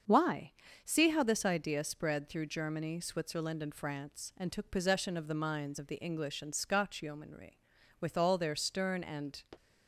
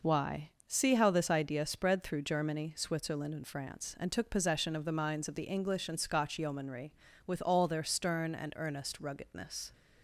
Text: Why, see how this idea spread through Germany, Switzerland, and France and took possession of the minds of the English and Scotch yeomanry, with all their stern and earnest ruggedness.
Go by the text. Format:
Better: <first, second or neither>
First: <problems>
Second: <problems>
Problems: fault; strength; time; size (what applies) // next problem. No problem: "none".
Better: second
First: starts louder than the rest; until 1.3 s; 7 dB // stops before "earnest ruggedness"; at 9.5 s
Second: none